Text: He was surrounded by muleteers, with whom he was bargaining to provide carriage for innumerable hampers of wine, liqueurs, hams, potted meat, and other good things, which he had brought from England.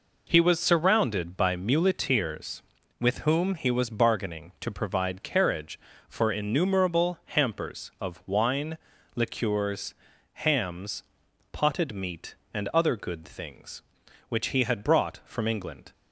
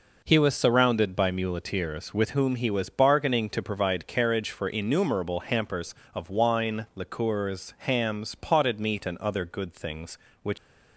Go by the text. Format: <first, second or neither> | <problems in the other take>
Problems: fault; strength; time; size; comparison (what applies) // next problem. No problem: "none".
first | stops before "he had brought from England"; at 10.5 s